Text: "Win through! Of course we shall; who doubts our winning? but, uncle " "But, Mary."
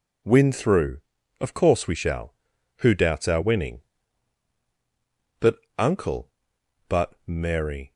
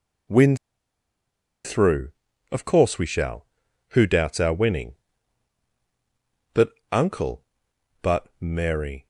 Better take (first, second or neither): first